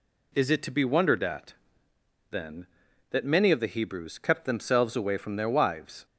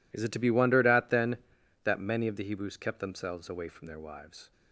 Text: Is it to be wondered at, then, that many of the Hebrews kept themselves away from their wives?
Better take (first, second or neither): first